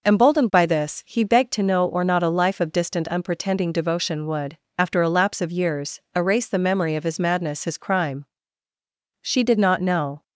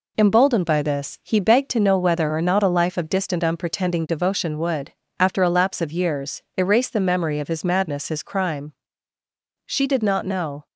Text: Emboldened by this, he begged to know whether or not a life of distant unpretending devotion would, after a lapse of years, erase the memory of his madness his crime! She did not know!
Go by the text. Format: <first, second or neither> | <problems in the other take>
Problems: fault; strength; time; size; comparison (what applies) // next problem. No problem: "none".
second | skips "whether"; at 1.8 s